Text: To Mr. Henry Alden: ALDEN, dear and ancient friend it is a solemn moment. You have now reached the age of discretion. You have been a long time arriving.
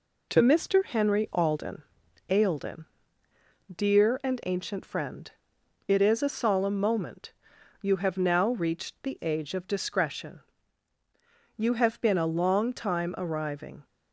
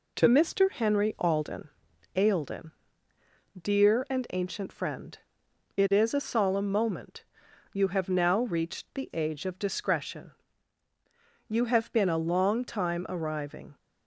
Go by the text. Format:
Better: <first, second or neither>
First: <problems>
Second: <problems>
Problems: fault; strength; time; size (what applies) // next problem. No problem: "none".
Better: neither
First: pauses between "friend" and "it"; noticeable; at 5.3 s; 0.56 s long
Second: pauses between "friend" and "it"; noticeable; at 5.1 s; 0.58 s long